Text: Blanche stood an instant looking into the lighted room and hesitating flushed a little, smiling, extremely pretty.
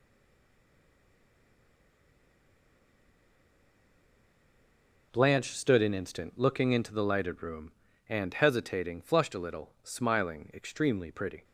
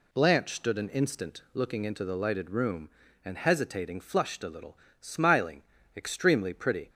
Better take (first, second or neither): second